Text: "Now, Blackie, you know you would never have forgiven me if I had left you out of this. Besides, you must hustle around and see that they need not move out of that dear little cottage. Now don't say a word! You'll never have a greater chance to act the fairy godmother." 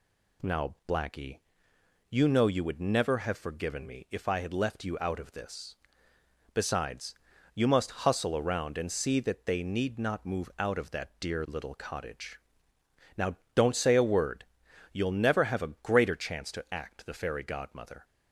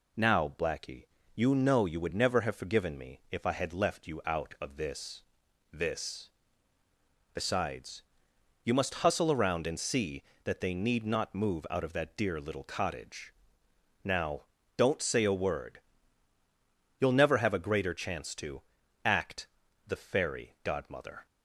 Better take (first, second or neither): first